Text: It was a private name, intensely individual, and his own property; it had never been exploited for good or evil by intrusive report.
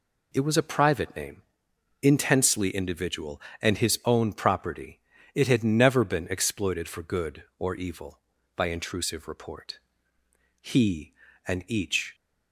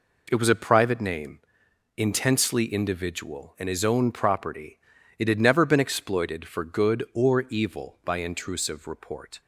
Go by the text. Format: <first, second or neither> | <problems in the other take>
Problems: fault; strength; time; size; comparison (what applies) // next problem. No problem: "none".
second | goes on to say "He and each"; from 10.5 s on; 1.5 s long